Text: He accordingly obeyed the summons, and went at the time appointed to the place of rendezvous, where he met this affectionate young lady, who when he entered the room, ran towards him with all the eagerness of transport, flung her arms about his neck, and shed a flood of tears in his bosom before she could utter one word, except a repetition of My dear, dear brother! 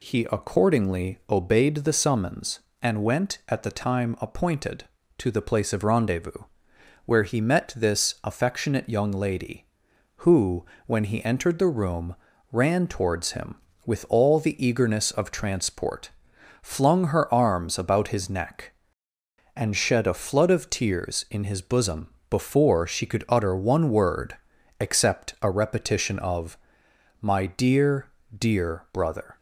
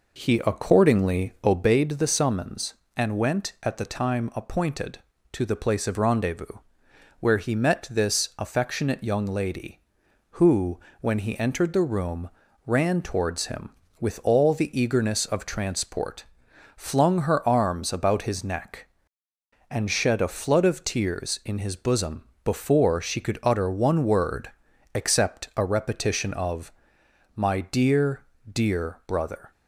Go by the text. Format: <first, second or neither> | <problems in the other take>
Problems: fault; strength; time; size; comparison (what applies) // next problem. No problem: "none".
first | starts louder than the rest; noticeable; until 1.8 s; 4.5 dB // pauses between "who" and "when"; slight; at 10.7 s; 0.22 s long; slight in the first // pauses between "bosom" and "before"; slight; at 22.2 s; 0.20 s long; slight in the first // pauses between "of" and "My"; noticeable; at 26.7 s; 0.62 s long; noticeable in the first